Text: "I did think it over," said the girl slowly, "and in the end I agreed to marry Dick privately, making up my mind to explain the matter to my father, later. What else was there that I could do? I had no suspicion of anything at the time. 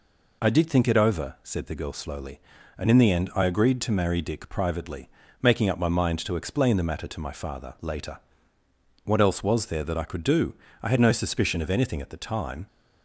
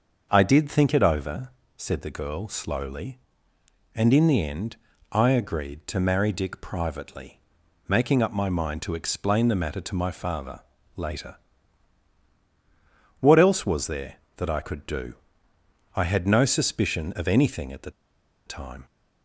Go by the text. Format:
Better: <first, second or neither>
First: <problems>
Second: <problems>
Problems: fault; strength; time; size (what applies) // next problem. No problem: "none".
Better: first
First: none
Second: starts louder than the rest; until 1.3 s; 6.5 dB // pauses between "end" and "I"; slight; at 4.7 s; 0.36 s long // pauses between "the" and "time"; noticeable; at 17.8 s; 0.56 s long